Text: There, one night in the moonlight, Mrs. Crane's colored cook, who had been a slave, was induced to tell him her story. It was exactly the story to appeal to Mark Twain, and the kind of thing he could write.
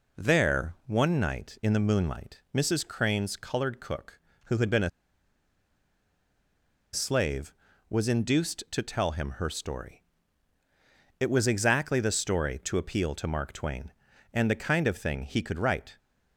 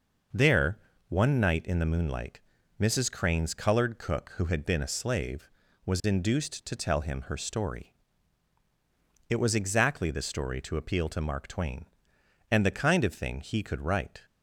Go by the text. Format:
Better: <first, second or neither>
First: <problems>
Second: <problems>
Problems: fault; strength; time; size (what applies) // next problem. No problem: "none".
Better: second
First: pauses between "a" and "slave"; strong; at 4.8 s; 2.0 s long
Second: none